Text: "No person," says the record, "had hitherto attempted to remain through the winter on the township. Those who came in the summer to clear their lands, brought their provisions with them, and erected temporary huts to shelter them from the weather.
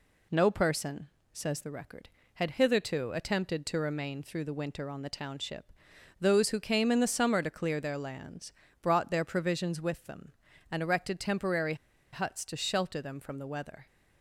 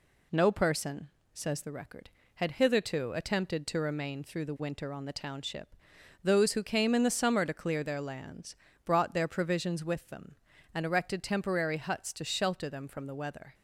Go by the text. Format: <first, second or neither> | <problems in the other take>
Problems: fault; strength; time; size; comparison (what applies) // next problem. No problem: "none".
second | pauses between "temporary" and "huts"; at 11.7 s; 0.38 s long